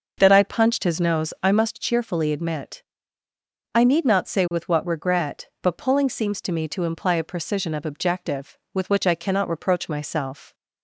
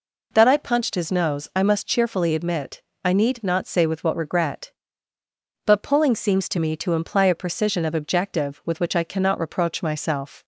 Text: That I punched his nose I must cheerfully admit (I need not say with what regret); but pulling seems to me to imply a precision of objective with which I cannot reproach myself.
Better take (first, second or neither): second